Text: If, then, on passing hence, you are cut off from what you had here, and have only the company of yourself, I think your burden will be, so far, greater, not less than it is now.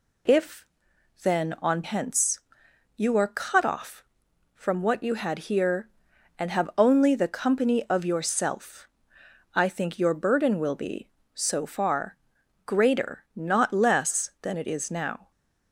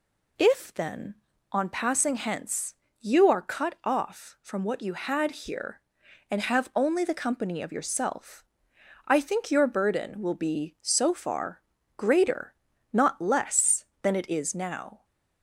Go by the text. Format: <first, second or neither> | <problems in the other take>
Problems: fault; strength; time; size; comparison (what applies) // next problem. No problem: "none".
second | skips "passing"; at 1.8 s